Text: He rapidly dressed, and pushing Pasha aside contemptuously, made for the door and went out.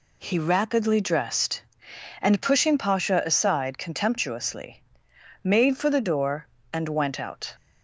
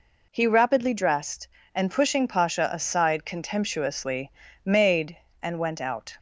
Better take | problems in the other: first | skips "for the door"; at 5.2 s

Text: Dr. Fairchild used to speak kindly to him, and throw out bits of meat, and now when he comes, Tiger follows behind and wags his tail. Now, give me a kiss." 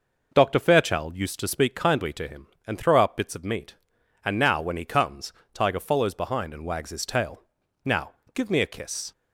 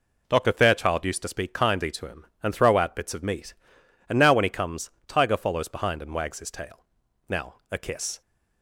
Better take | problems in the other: first | skips "give me"; at 7.6 s

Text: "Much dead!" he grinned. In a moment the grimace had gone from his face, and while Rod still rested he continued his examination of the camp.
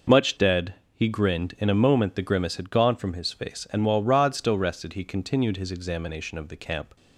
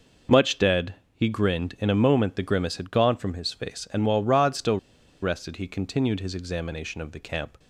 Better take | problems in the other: first | pauses between "still" and "rested"; at 4.7 s; 0.44 s long

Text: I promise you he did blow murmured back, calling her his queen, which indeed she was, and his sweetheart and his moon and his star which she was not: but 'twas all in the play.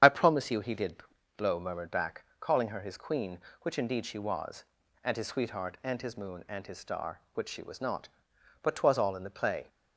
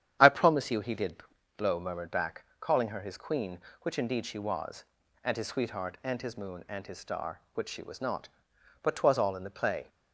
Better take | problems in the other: second | loses the start of "I"; at 0.0 s; 25 ms // starts louder than the rest; strong; until 1.4 s; 9 dB; strong in the second // pauses between "did" and "blow"; at 0.9 s; 0.40 s long; also in the second

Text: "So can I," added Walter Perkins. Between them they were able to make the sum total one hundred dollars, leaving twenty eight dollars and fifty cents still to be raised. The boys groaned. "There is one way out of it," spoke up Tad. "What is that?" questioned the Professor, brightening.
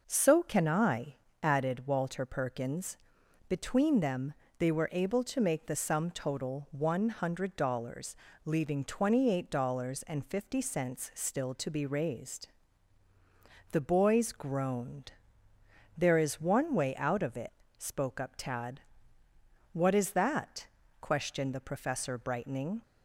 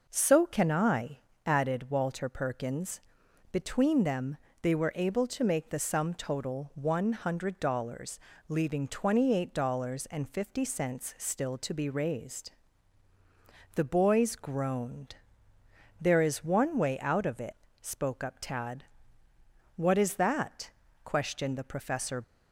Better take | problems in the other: first | pauses between "them" and "they"; slight; at 4.3 s; 0.24 s long; slight in the first // stops before "brightening"; at 22.2 s

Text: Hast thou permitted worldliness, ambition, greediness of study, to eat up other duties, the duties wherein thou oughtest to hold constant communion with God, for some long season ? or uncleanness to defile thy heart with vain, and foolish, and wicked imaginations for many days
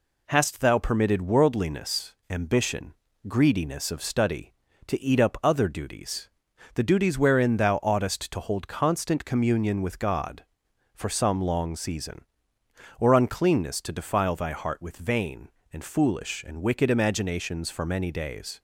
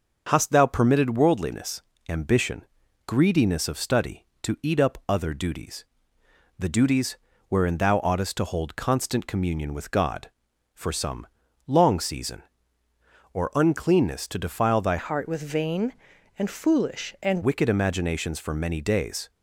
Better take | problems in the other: first | starts louder than the rest; until 1.2 s; 6.5 dB // pauses between "duties" and "wherein"; slight; at 7.1 s; 0.32 s long // pauses between "some" and "long"; at 11.2 s; 0.40 s long // changes voice from "heart" to "and"; from 14.9 to 17.4 s; 2.5 s long

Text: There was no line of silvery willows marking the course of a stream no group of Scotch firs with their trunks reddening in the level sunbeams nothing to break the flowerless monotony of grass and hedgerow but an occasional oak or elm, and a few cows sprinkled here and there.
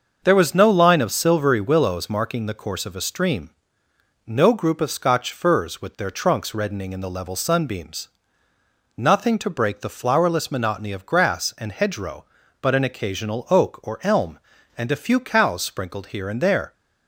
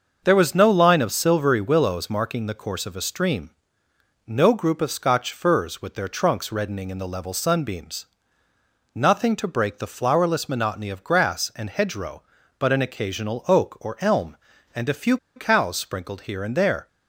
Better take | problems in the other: first | starts louder than the rest; until 1.2 s; 6.5 dB; also in the first // pauses between "stream" and "no"; noticeable; at 3.5 s; 0.74 s long; noticeable in the first // pauses between "sunbeams" and "nothing"; noticeable; at 8.0 s; 0.90 s long; noticeable in the first // pauses between "few" and "cows"; slight; at 15.1 s; 0.19 s long

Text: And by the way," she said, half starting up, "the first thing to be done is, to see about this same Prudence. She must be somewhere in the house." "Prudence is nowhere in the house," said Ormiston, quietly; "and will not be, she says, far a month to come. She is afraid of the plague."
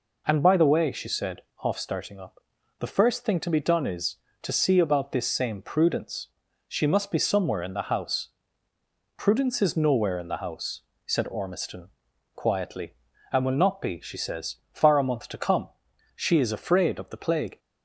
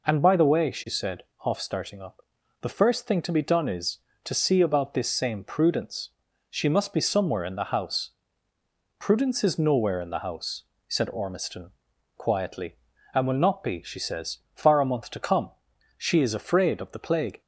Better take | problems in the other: neither | none

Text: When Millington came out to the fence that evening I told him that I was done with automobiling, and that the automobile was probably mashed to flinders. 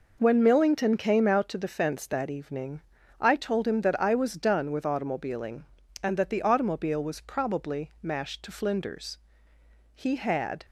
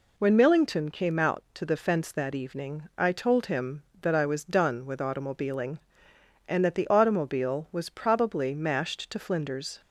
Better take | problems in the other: second | pauses between "evening" and "I"; at 2.8 s; 0.40 s long // goes on to say "He had"; noticeable; from 9.9 s on; 0.70 s long

